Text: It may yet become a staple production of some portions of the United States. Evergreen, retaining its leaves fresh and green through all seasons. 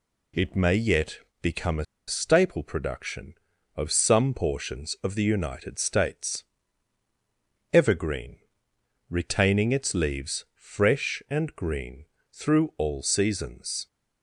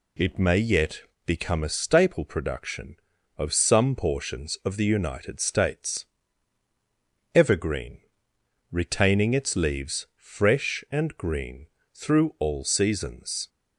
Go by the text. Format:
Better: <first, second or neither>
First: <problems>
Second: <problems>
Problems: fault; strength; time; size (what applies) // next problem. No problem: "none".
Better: second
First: pauses between "yet" and "become"; slight; at 1.2 s; 0.22 s long // pauses between "a" and "staple"; slight; at 1.8 s; 0.23 s long // pauses between "green" and "through"; slight; at 12.0 s; 0.26 s long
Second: pauses between "yet" and "become"; slight; at 1.0 s; 0.23 s long // pauses between "green" and "through"; slight; at 11.6 s; 0.26 s long